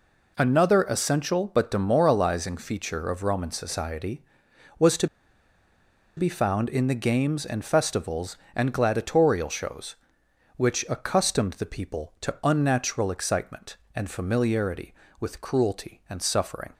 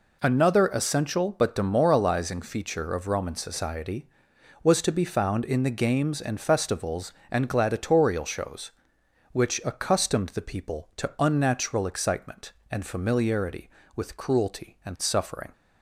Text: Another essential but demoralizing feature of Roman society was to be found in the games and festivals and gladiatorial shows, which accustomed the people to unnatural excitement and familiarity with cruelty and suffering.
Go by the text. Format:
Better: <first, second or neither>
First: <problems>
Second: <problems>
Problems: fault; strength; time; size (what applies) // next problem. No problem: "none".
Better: second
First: pauses between "to" and "be"; at 5.0 s; 1.1 s long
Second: none